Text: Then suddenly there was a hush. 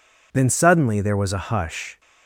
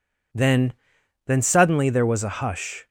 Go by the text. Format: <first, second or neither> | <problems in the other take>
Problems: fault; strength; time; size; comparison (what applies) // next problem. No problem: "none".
first | says "Then" twice; at 1.2 s